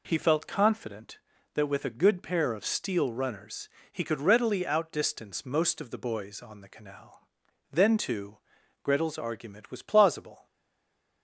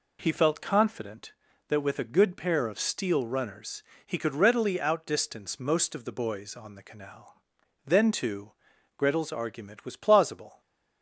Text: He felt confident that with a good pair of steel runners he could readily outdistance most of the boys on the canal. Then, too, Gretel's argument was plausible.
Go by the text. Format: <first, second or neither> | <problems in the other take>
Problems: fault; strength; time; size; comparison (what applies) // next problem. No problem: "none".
second | pauses between "runners" and "he"; slight; at 3.6 s; 0.24 s long; slight in the second // stays silent after the last word; slight; from 10.4 s on; 0.8 s long